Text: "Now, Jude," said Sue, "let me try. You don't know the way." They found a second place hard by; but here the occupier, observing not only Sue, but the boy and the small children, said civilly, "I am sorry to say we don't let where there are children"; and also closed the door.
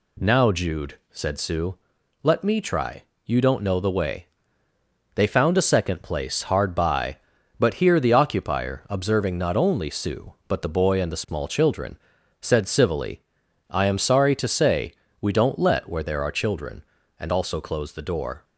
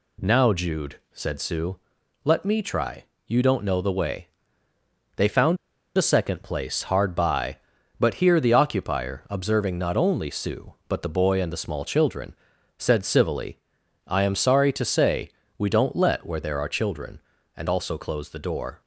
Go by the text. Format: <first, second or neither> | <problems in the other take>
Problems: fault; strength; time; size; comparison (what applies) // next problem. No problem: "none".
first | pauses between "found" and "a"; at 5.5 s; 0.39 s long // pauses between "say" and "we"; slight; at 15.3 s; 0.28 s long; slight in the first